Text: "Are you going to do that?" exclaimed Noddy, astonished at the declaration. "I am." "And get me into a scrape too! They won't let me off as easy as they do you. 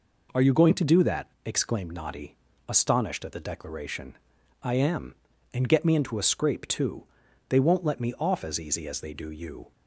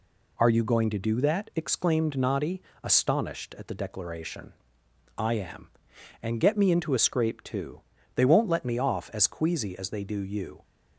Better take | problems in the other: first | says "queasy" for "easy"; at 9.2 s

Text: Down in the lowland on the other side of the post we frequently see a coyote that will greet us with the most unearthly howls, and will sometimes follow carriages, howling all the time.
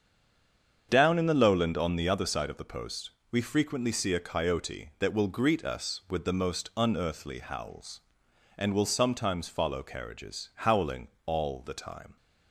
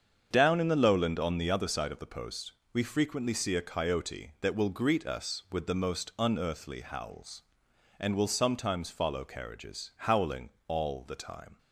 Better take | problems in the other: second | stays silent before the first word; slight; until 0.8 s; 0.8 s long // starts louder than the rest; strong; until 1.9 s; 7.5 dB; strong in the second // pauses between "post" and "we"; slight; at 3.1 s; 0.18 s long; slight in the second // pauses between "howling" and "all"; slight; at 11.0 s; 0.20 s long; slight in the second

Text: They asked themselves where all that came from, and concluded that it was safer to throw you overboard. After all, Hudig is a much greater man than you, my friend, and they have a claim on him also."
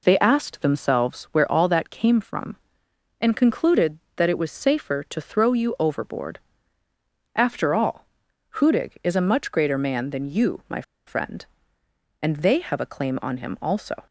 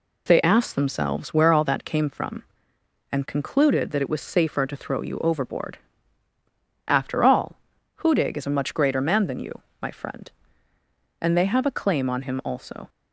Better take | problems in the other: second | pauses between "my" and "friend"; slight; at 10.8 s; 0.24 s long

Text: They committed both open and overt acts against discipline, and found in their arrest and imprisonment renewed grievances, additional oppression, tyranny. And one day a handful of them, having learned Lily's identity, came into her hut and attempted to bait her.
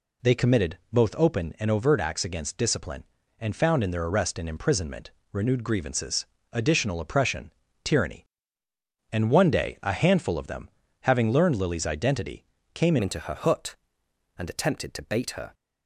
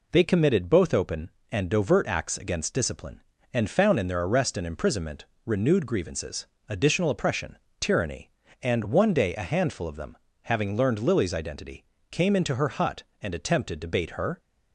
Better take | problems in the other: second | pauses between "imprisonment" and "renewed"; slight; at 5.1 s; 0.20 s long; slight in the second // changes voice at "into"; from 13.0 s on; 2.5 s long

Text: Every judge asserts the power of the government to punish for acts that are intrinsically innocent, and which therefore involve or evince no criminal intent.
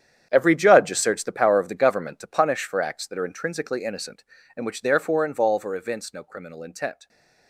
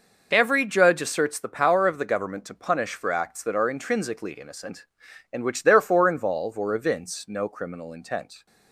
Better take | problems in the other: second | gets quieter; strong; throughout; 14 dB

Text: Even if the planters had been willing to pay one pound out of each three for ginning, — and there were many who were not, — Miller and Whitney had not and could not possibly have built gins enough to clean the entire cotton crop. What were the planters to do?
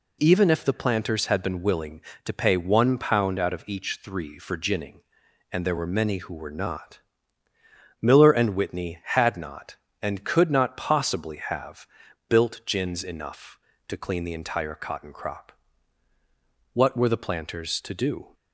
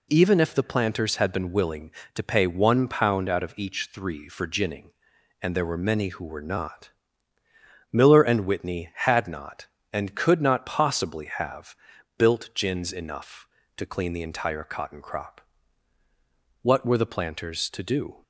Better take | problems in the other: neither | pauses between "have" and "built"; the same in both

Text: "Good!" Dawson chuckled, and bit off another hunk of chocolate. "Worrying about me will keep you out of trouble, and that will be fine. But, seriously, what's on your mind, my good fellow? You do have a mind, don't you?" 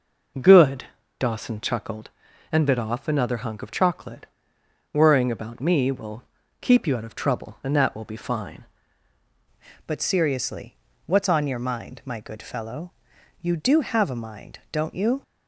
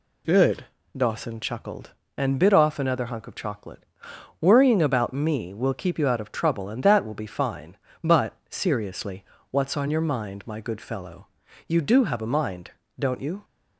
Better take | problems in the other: second | pauses between "will" and "keep"; at 6.2 s; 0.40 s long // changes voice at "But"; from 9.8 s on; 5.4 s long

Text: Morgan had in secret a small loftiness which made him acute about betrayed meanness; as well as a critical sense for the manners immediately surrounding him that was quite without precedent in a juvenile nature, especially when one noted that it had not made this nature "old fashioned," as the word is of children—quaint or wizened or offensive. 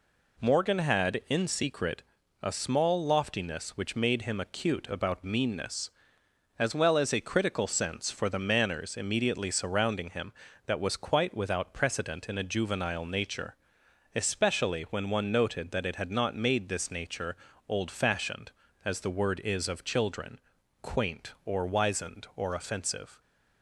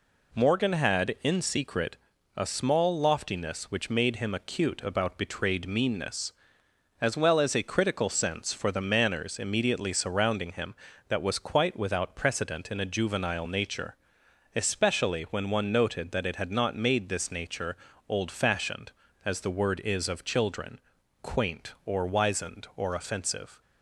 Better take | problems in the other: second | pauses between "secret" and "a"; at 2.0 s; 0.42 s long; also in the second // skips "betrayed"; at 5.2 s // pauses between "nature" and "old"; slight; at 17.3 s; 0.32 s long; slight in the second

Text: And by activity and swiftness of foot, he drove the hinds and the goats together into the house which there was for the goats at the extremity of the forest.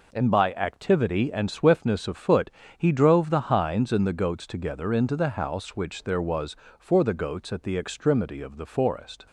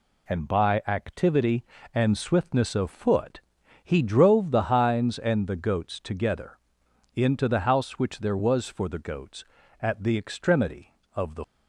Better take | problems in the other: first | pauses between "together" and "into"; noticeable; at 6.5 s; 0.56 s long // stops before "forest"; at 11.4 s

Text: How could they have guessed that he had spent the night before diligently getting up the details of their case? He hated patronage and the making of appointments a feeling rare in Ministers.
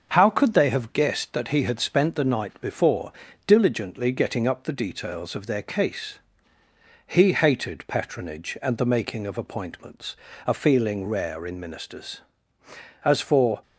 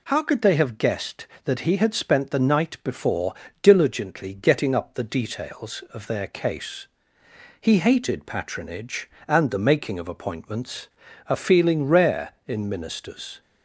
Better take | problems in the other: second | starts louder than the rest; until 1.1 s; 6 dB // pauses between "before" and "diligently"; slight; at 3.1 s; 0.34 s long; slight in the second // pauses between "appointments" and "a"; slight; at 10.1 s; 0.30 s long; also in the second // goes on to say "As for"; from 13.0 s on; 0.58 s long

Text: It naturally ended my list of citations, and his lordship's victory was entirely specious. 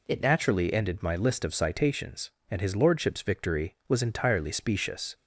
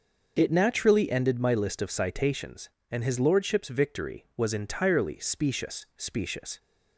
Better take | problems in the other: first | starts louder than the rest; until 1.3 s; 6.5 dB // says "specious" twice; at 5.9 s

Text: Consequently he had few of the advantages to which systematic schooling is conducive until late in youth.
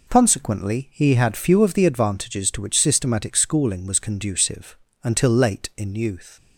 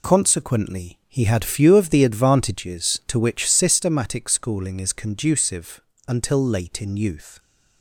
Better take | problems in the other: second | says "was" for "is"; at 3.8 s // pauses between "conducive" and "until"; slight; at 4.7 s; 0.26 s long; slight in the second

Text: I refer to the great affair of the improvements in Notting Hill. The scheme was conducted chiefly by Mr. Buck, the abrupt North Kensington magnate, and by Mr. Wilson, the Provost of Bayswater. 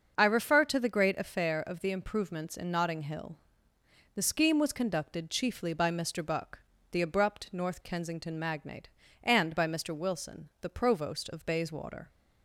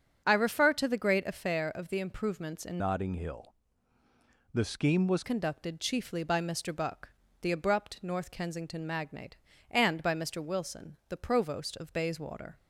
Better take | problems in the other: first | starts louder than the rest; until 1.2 s; 7 dB; also in the first // changes voice from "Notting" to "was"; from 2.7 to 5.2 s; 2.5 s long

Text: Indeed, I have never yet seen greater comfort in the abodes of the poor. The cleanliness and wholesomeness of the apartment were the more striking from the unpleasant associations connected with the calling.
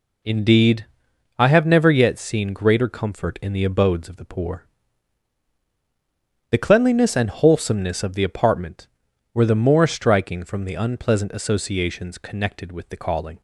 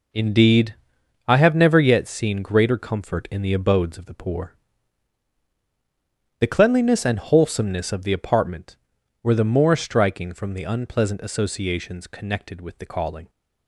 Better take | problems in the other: first | gets quieter; strong; throughout; 10 dB

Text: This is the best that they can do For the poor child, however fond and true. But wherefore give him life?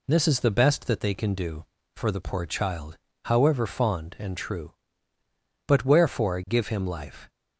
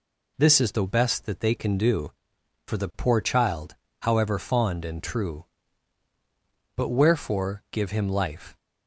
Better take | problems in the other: neither | none

